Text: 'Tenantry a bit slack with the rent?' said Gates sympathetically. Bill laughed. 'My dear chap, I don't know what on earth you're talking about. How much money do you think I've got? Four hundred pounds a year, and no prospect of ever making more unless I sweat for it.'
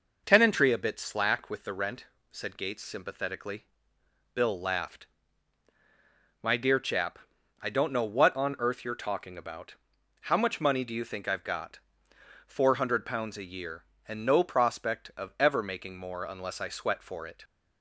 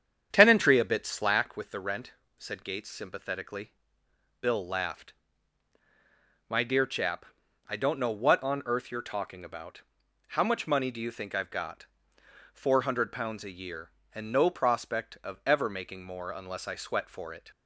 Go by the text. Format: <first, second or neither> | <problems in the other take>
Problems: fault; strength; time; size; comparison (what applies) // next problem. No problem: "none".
first | starts louder than the rest; strong; until 1.4 s; 8 dB